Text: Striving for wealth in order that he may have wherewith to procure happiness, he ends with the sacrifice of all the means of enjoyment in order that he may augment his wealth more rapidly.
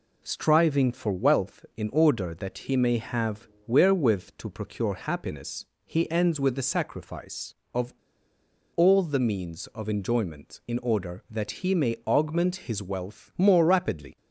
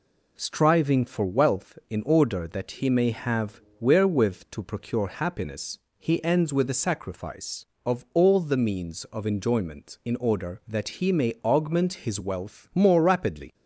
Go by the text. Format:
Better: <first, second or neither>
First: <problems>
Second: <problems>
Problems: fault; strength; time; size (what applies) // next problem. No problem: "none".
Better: second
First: pauses between "have" and "wherewith"; slight; at 3.4 s; 0.18 s long // pauses between "of" and "all"; noticeable; at 7.9 s; 0.83 s long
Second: pauses between "have" and "wherewith"; slight; at 3.6 s; 0.18 s long